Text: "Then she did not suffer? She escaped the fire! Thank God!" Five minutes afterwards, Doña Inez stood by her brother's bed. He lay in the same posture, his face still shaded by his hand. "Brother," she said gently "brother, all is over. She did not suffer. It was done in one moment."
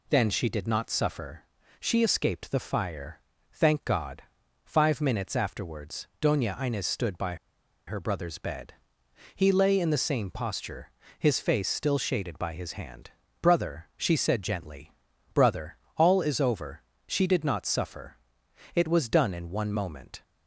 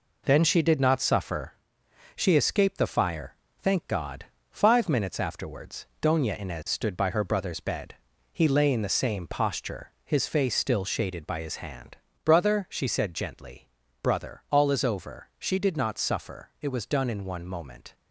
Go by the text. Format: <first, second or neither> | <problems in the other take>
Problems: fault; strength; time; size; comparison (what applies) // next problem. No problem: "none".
second | pauses between "by" and "her"; noticeable; at 7.3 s; 0.52 s long // pauses between "gently" and "brother"; at 14.9 s; 0.42 s long; slight in the second